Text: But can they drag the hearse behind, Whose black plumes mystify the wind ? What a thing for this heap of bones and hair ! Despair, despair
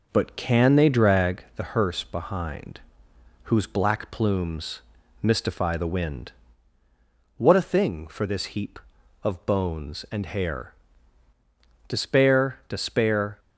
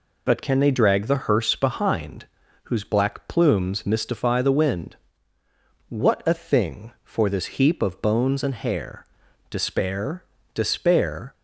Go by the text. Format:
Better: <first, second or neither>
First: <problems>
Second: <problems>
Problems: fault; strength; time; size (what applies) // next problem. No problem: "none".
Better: second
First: starts louder than the rest; noticeable; until 1.5 s; 5.5 dB // pauses between "plumes" and "mystify"; at 4.8 s; 0.42 s long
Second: none